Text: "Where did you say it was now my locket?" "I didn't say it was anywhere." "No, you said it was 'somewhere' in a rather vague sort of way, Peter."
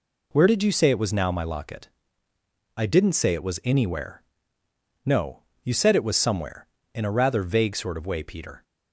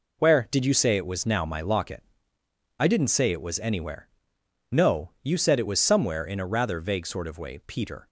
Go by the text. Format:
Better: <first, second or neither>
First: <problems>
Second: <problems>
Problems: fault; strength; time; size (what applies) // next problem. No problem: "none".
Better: neither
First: none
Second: none